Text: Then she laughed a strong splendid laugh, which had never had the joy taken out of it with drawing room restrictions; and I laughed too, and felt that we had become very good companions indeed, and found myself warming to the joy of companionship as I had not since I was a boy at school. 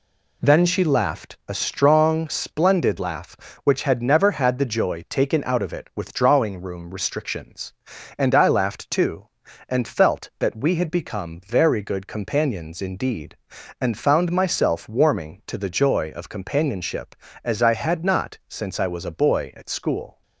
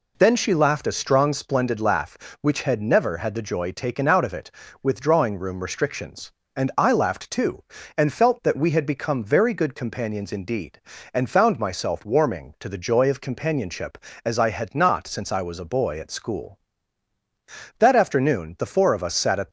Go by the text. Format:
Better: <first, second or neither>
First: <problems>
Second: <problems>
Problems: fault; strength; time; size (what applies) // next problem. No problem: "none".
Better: first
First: none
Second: goes on to say "That afternoon the four of us sat at"; strong; from 17.7 s on; 1.7 s long